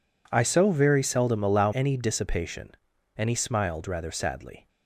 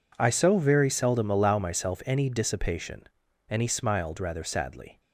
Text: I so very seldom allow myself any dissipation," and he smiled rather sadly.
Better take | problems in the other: second | skips "myself"; at 1.7 s

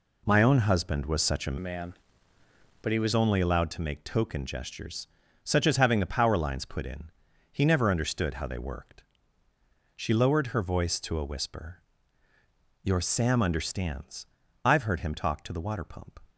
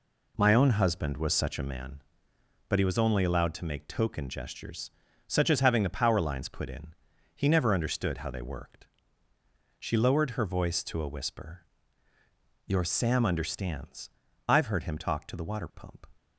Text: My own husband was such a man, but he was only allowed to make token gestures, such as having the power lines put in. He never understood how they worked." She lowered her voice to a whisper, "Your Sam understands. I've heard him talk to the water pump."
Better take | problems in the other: second | changes voice from "man" to "was"; from 1.5 to 3.1 s; 1.6 s long

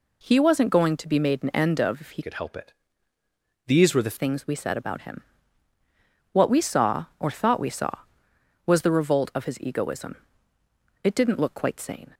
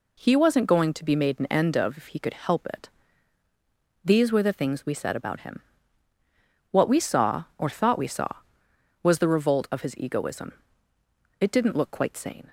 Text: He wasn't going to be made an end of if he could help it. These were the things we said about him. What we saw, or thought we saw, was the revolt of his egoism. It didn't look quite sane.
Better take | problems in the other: second | changes voice from "could" to "the"; from 2.2 to 4.1 s; 1.9 s long

